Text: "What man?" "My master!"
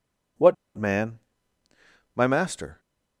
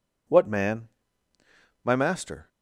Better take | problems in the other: second | pauses between "What" and "man"; slight; at 0.5 s; 0.20 s long

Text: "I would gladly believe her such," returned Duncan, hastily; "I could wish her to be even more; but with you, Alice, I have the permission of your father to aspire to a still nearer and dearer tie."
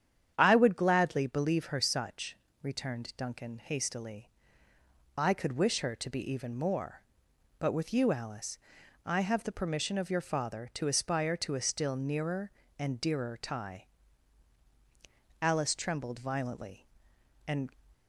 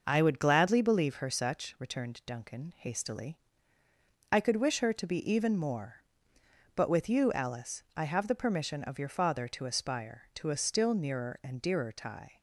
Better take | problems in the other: second | starts louder than the rest; strong; until 1.3 s; 9 dB // goes on to say "Alice trembled violently and"; strong; from 15.4 s on; 2.2 s long

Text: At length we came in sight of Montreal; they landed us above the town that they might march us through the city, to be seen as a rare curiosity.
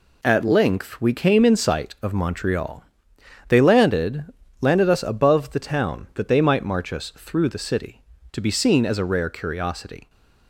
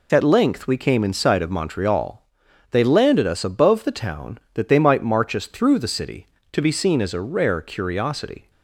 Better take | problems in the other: second | says "landed" twice; at 4.5 s

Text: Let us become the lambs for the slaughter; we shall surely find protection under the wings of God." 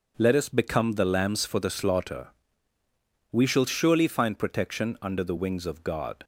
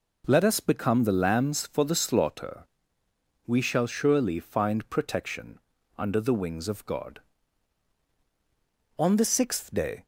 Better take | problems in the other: first | pauses between "protection" and "under"; at 5.5 s; 0.40 s long // goes on to say "On the sixth day"; noticeable; from 8.9 s on; 1.0 s long

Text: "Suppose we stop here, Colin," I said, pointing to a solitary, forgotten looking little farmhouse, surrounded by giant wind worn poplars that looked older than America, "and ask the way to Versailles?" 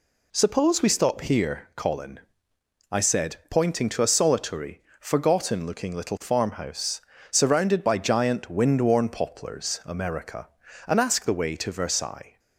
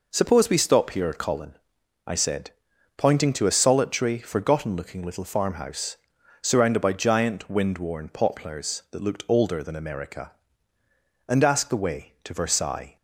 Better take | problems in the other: second | skips "that looked older than"; at 9.8 s

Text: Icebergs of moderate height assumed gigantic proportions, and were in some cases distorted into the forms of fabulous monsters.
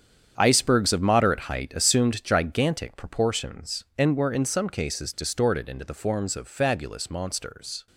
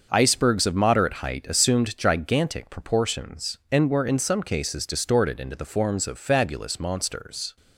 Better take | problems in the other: second | gets quieter; strong; throughout; 11 dB // starts louder than the rest; strong; until 1.3 s; 8.5 dB; also in the second

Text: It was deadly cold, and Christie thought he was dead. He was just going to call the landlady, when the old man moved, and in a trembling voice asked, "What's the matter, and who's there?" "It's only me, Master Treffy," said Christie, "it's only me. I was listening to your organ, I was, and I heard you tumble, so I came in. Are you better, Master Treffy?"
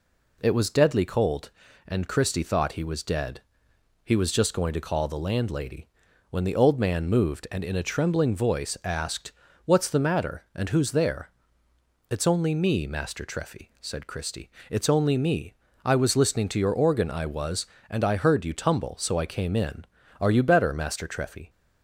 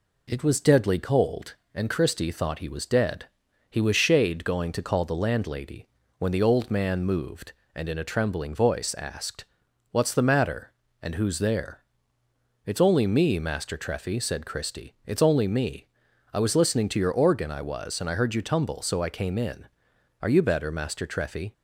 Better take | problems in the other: first | says "shade" for "just"; at 3.9 s

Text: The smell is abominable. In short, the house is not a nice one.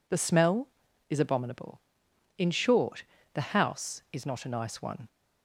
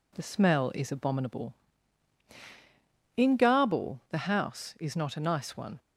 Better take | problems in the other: first | says "garble" for "short"; at 3.3 s

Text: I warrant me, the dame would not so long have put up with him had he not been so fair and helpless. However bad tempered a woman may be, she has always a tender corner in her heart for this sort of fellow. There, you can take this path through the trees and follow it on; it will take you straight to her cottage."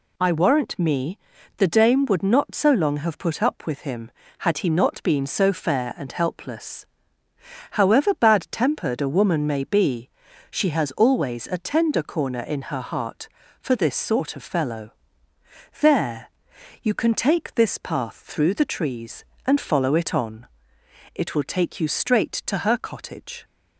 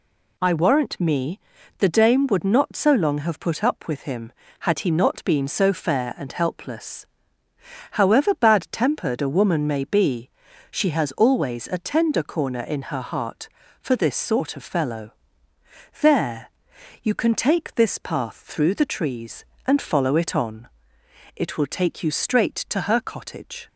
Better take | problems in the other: neither | none

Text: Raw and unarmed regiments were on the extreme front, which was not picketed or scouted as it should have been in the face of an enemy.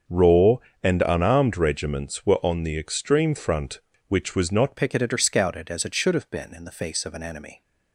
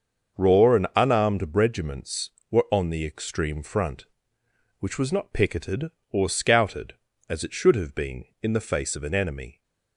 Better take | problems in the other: second | starts louder than the rest; until 1.3 s; 7 dB; also in the second // changes voice at "picketed"; from 4.7 s on; 2.9 s long

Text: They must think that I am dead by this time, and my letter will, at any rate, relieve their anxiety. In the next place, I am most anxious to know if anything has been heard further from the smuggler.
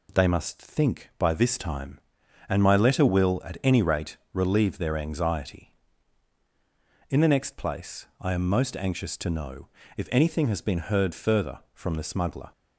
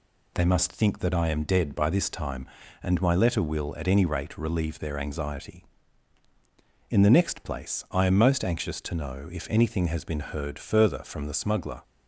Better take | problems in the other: second | skips "that I am dead"; at 1.1 s // pauses between "know" and "if"; slight; at 9.6 s; 0.28 s long

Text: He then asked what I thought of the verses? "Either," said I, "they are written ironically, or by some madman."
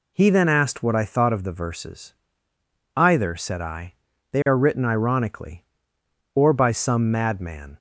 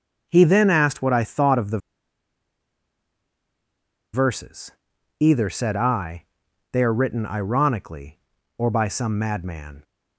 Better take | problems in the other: first | starts louder than the rest; until 1.3 s; 6.5 dB // pauses between "the" and "verses"; strong; at 1.7 s; 2.3 s long

